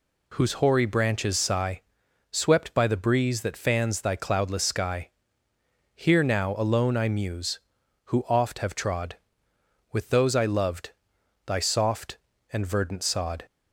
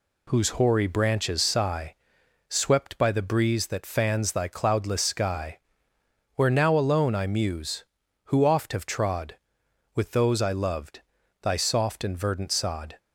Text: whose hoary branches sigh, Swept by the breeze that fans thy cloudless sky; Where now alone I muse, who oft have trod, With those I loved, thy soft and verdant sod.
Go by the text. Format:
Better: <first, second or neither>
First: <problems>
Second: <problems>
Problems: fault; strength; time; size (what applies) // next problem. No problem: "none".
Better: second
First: says "Here" for "Where"; at 5.9 s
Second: none